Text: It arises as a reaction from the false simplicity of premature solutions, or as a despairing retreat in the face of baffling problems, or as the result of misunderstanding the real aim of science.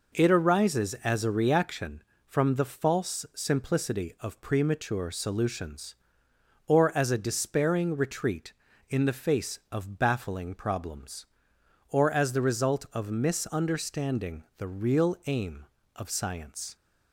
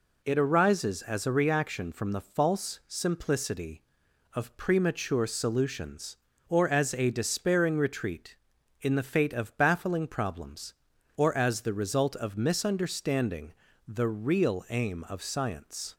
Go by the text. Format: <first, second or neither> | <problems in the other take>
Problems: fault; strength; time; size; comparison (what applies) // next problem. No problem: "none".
first | says "fate" for "face"; at 9.0 s // pauses between "misunderstanding" and "the"; slight; at 13.5 s; 0.36 s long; slight in the first